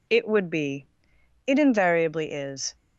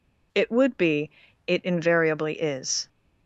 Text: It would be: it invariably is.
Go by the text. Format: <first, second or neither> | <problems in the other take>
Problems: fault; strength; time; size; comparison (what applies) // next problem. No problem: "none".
neither | none